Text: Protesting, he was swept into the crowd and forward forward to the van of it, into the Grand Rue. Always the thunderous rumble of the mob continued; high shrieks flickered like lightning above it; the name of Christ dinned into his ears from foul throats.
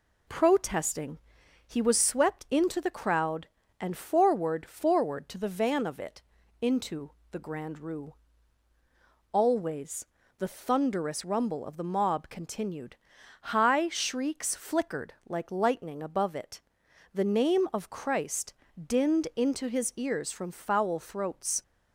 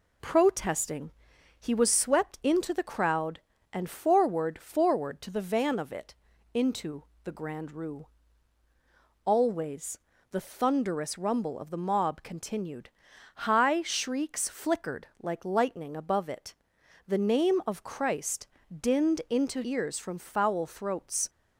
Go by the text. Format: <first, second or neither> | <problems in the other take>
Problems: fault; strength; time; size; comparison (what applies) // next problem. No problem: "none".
first | pauses between "into" and "the"; slight; at 7.0 s; 0.20 s long; slight in the first // pauses between "Always" and "the"; slight; at 9.9 s; 0.34 s long; slight in the first // pauses between "Christ" and "dinned"; slight; at 18.4 s; 0.32 s long; slight in the first // skips "his"; at 19.6 s